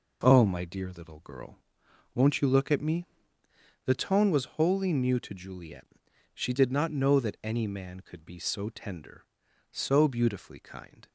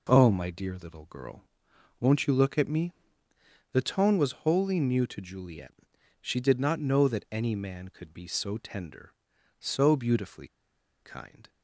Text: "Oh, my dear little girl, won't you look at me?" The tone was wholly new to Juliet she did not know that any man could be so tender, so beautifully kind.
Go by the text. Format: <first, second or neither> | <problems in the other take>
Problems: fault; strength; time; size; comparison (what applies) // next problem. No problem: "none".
first | pauses between "Juliet" and "she"; noticeable; at 5.7 s; 0.48 s long; noticeable in the first // pauses between "beautifully" and "kind"; noticeable; at 10.4 s; 0.54 s long